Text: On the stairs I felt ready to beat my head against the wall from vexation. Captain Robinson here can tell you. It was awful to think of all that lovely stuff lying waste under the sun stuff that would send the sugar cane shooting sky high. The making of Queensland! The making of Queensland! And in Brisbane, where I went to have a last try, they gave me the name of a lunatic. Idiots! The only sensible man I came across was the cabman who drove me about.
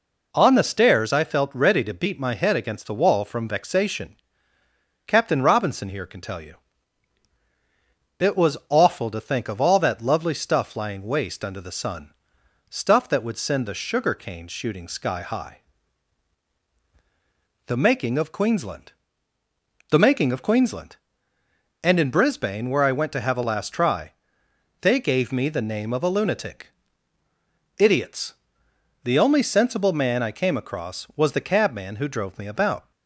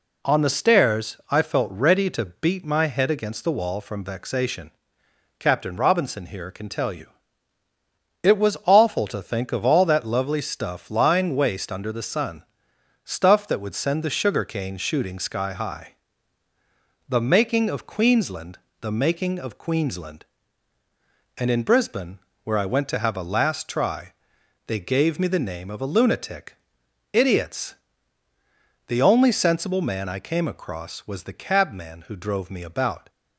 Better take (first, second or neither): neither